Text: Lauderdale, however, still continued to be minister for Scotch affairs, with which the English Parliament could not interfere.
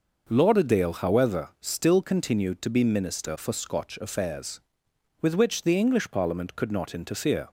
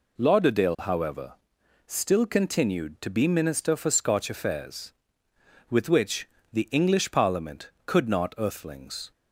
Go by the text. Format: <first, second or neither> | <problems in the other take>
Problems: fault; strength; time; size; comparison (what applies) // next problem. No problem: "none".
first | pauses between "which" and "the"; slight; at 6.2 s; 0.24 s long // says "earthlings" for "interfere"; at 8.3 s